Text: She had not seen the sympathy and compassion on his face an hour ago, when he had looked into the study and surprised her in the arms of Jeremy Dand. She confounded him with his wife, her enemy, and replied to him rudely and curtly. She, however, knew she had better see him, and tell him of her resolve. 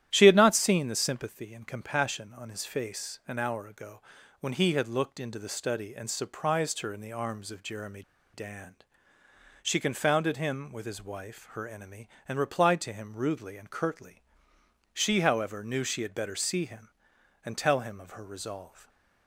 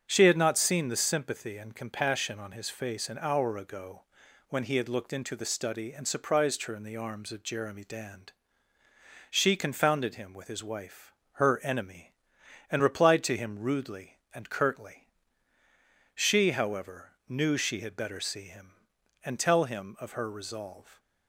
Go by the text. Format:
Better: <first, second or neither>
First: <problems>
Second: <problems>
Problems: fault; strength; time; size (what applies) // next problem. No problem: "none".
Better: second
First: starts louder than the rest; strong; until 1.1 s; 11.5 dB // pauses between "Jeremy" and "Dand"; slight; at 8.0 s; 0.31 s long // stays silent after the last word; slight; from 18.6 s on; 0.6 s long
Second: starts louder than the rest; strong; until 1.1 s; 7.5 dB